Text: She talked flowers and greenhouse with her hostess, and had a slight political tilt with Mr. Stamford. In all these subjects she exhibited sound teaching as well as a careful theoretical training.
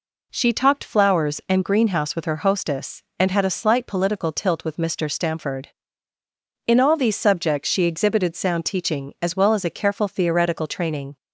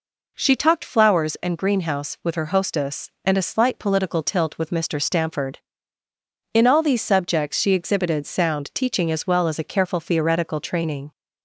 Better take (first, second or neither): first